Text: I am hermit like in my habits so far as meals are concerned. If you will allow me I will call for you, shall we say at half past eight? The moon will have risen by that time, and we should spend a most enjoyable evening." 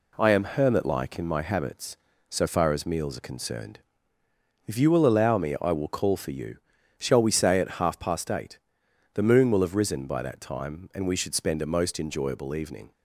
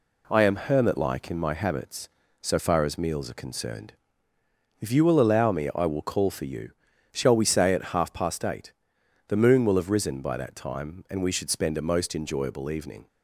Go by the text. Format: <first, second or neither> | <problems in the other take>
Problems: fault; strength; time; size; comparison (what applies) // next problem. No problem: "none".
neither | none